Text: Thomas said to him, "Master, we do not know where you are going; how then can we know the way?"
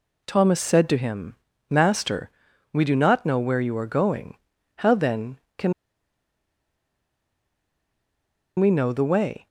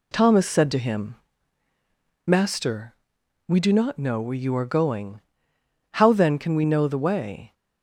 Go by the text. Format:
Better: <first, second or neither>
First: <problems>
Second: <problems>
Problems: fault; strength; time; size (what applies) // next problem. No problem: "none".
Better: second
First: pauses between "can" and "we"; strong; at 5.7 s; 2.8 s long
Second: none